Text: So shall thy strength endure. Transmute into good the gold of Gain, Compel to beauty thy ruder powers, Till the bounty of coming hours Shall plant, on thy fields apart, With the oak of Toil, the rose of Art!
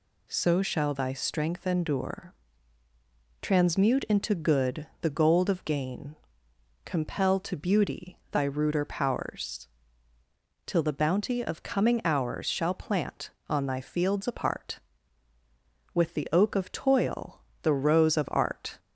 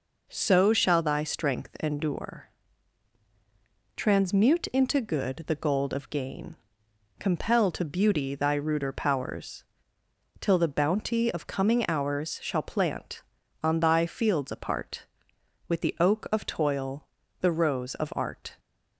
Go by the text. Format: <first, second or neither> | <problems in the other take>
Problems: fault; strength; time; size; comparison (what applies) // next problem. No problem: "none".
neither | none